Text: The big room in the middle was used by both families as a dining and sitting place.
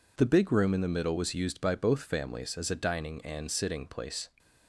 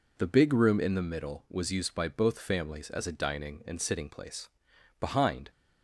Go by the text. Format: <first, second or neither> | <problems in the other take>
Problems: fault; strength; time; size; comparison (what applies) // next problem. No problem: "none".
first | goes on to say "Behind"; from 4.9 s on; 0.50 s long